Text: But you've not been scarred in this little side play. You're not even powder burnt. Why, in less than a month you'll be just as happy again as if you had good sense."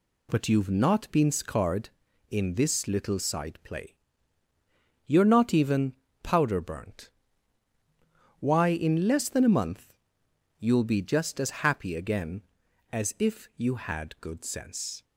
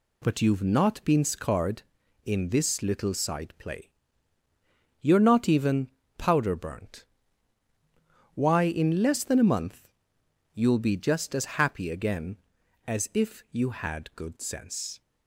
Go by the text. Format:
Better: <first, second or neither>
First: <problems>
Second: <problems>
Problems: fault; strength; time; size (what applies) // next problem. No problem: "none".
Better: neither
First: pauses between "even" and "powder"; slight; at 5.9 s; 0.28 s long // pauses between "month" and "you'll"; noticeable; at 9.9 s; 0.66 s long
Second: pauses between "even" and "powder"; slight; at 5.8 s; 0.28 s long // pauses between "month" and "you'll"; noticeable; at 9.8 s; 0.66 s long